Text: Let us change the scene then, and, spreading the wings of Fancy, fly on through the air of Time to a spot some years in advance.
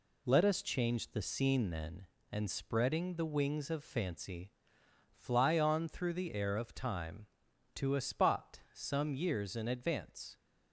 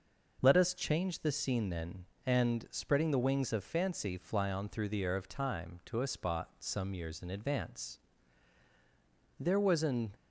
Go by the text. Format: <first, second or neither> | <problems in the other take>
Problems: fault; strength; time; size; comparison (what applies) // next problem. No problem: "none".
first | goes on to say "There was an"; noticeable; from 9.3 s on; 0.74 s long